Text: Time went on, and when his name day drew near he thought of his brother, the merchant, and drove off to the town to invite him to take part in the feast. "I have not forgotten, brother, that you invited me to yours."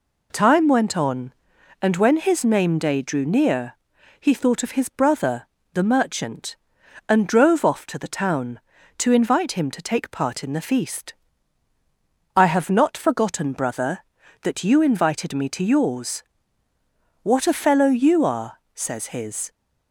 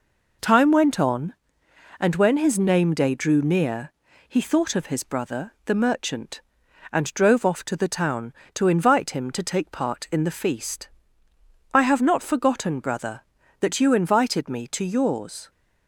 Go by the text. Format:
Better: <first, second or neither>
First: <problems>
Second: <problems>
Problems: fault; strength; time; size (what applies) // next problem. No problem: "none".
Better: second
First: pauses between "near" and "he"; noticeable; at 3.7 s; 0.46 s long // goes on to say "What a fellow you are says his"; strong; from 17.2 s on; 2.2 s long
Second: pauses between "near" and "he"; slight; at 3.9 s; 0.34 s long